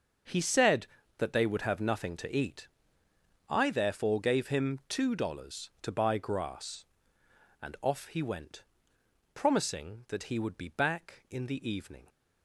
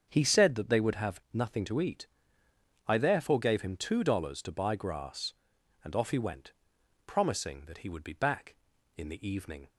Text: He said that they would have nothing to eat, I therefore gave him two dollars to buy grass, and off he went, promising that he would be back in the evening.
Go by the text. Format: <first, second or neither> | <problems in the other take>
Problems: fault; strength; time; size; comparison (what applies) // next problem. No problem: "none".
neither | starts louder than the rest; the same in both